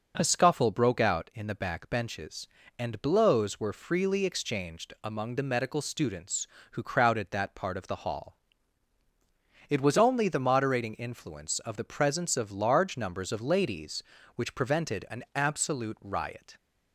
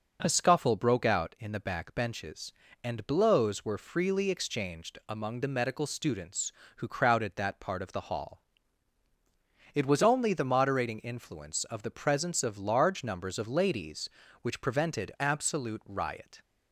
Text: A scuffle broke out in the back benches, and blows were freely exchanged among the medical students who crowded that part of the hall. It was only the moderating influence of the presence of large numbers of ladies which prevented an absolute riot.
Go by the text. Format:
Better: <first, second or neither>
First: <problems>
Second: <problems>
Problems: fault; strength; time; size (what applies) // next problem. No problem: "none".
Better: first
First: none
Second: skips "an"; at 15.1 s